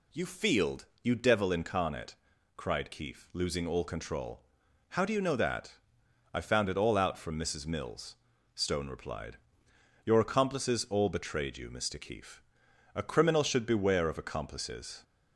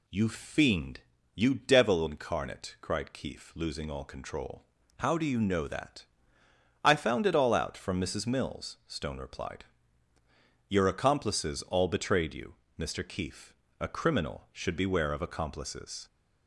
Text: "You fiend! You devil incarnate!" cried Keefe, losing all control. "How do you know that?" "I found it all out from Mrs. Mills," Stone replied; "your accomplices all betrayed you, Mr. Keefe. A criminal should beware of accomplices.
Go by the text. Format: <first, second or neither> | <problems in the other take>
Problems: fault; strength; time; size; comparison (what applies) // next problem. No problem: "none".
second | says "field" for "fiend"; at 0.2 s